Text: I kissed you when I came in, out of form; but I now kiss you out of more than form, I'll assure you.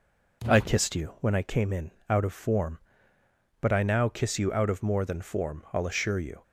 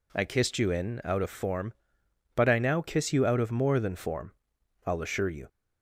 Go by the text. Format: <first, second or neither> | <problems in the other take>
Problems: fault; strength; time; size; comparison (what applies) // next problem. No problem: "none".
first | skips "when I came"; at 0.7 s